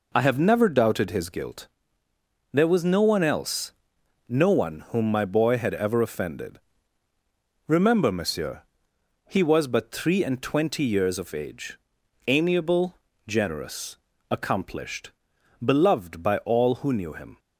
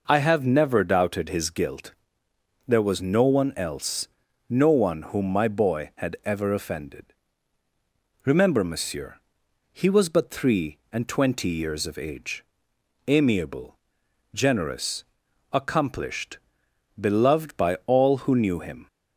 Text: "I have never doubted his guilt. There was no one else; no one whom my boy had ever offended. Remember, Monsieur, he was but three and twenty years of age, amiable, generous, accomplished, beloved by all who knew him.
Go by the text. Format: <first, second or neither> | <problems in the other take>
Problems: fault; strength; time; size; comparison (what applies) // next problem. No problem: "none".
neither | none